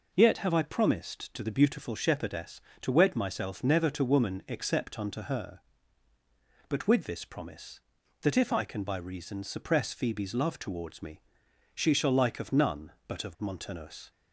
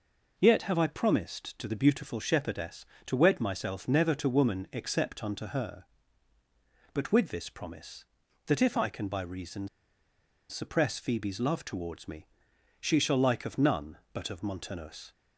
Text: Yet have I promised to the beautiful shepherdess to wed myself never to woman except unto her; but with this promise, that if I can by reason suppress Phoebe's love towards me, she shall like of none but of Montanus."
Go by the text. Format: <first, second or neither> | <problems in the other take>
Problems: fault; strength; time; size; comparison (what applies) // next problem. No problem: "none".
first | pauses between "reason" and "suppress"; noticeable; at 9.6 s; 0.82 s long